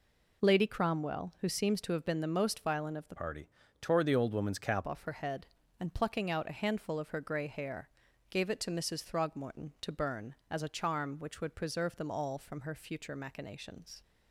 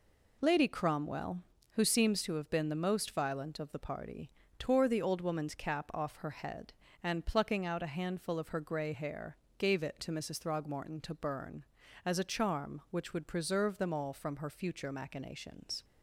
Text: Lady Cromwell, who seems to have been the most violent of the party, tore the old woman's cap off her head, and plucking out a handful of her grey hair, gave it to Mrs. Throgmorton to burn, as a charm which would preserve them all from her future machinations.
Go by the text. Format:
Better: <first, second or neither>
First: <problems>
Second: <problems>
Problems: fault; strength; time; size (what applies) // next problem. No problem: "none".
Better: second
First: changes voice from "party" to "cap"; from 3.1 to 4.8 s; 1.7 s long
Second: none